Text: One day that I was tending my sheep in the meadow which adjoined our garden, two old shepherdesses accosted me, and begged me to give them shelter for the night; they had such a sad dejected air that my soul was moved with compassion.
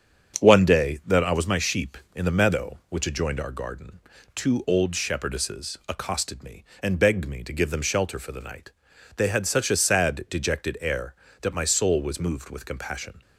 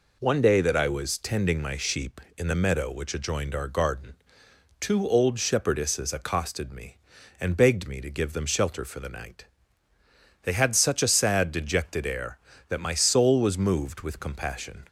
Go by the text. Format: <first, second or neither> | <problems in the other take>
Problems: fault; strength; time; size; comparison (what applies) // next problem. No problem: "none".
second | starts louder than the rest; strong; until 1.4 s; 7.5 dB // skips "tending"; at 1.4 s